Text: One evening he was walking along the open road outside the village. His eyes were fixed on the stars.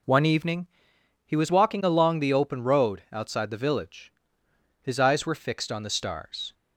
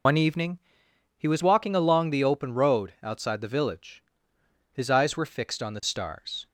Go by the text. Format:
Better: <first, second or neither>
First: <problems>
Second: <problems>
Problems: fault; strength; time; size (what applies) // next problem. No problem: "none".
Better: first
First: pauses between "evening" and "he"; noticeable; at 0.6 s; 0.58 s long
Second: loses the start of "One"; at 0.0 s; 90 ms // pauses between "evening" and "he"; noticeable; at 0.5 s; 0.58 s long